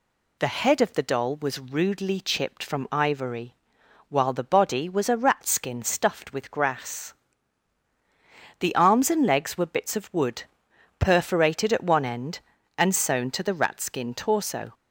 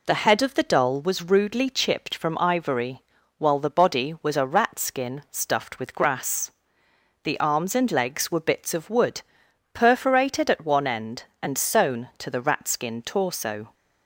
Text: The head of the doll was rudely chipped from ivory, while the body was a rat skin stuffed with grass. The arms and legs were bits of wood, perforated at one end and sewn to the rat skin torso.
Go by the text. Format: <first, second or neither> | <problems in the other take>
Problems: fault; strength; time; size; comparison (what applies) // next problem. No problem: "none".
neither | none